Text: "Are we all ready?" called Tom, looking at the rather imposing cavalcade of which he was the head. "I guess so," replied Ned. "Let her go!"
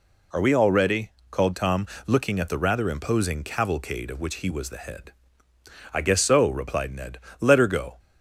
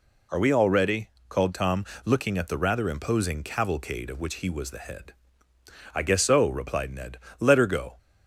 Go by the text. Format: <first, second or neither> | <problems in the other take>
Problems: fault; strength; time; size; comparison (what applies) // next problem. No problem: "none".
neither | none